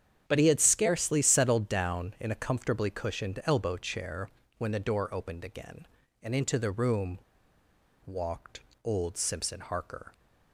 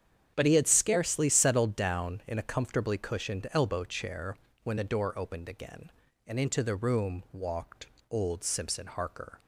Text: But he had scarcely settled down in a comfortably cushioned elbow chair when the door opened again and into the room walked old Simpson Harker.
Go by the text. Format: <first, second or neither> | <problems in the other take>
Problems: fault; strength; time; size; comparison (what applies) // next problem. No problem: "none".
second | starts louder than the rest; strong; until 1.2 s; 9 dB; strong in the second // pauses between "chair" and "when"; slight; at 4.2 s; 0.30 s long; slight in the second // pauses between "room" and "walked"; noticeable; at 7.1 s; 0.88 s long // pauses between "walked" and "old"; slight; at 8.6 s; 0.22 s long; slight in the second